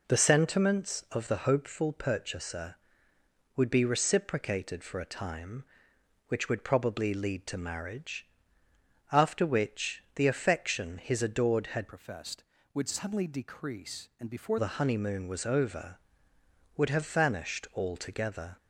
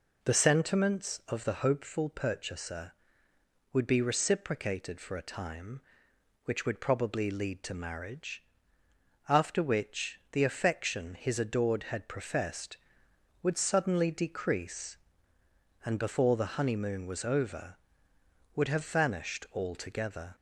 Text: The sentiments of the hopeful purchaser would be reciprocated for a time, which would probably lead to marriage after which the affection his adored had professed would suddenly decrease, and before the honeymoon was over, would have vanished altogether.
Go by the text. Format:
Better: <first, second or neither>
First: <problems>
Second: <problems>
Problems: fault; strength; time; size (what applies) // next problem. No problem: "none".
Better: second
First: pauses between "marriage" and "after"; noticeable; at 8.2 s; 0.84 s long // changes voice from "professed" to "before"; from 11.8 to 14.5 s; 2.7 s long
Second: pauses between "marriage" and "after"; noticeable; at 8.4 s; 0.84 s long